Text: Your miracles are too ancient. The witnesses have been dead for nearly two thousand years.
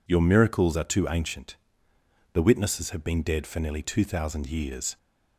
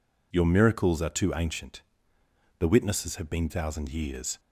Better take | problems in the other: first | skips "dead for nearly two"; at 3.4 s

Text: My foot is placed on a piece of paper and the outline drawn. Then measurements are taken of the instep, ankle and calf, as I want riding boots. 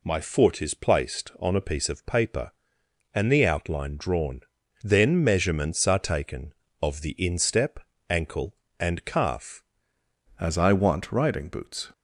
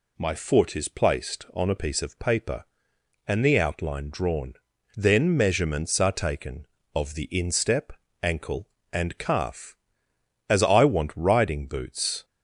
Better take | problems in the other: second | changes voice at "as"; from 10.3 s on; 1.6 s long

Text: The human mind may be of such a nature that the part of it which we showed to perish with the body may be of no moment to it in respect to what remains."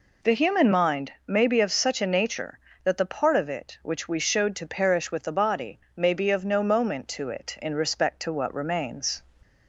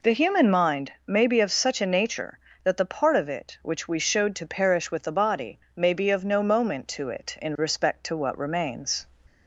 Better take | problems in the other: neither | pauses between "body" and "may"; slight; the same in both

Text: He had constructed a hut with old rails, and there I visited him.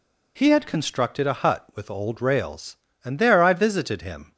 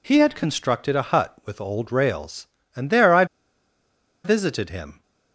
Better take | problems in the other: first | pauses between "I" and "visited"; at 3.2 s; 0.99 s long

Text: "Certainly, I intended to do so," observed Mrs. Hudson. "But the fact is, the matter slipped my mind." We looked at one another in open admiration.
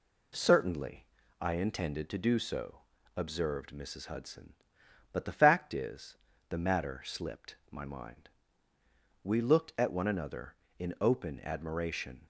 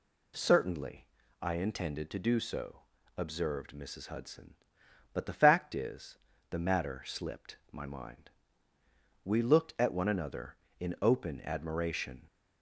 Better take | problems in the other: second | gets quieter; slight; throughout; 3 dB // pauses between "slipped" and "my"; slight; at 7.5 s; 0.16 s long; slight in the second

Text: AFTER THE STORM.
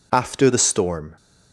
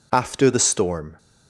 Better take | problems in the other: neither | none

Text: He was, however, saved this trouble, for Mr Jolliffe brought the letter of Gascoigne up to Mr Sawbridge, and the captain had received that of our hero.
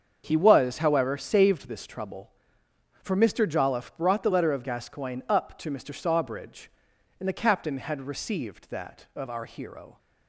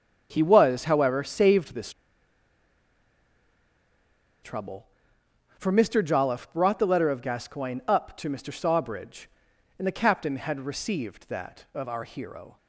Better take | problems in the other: first | starts louder than the rest; until 1.3 s; 7 dB; also in the first // pauses between "this" and "trouble"; strong; at 1.9 s; 2.5 s long

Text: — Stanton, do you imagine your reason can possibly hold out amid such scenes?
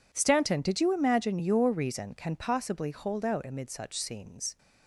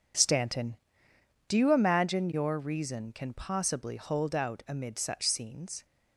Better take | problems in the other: second | says "did" for "do"; at 0.5 s

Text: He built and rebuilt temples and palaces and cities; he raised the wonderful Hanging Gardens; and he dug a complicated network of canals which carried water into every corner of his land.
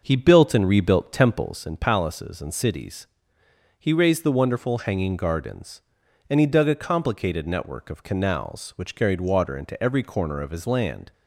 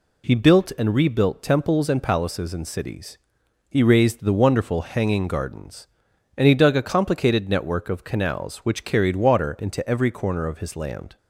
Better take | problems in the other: second | starts louder than the rest; until 1.6 s; 6 dB

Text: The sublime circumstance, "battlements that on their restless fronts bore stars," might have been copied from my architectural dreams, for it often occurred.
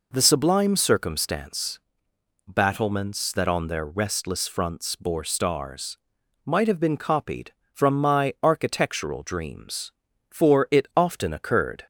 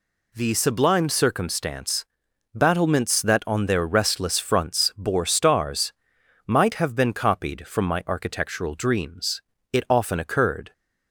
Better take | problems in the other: first | skips "for"; at 9.5 s

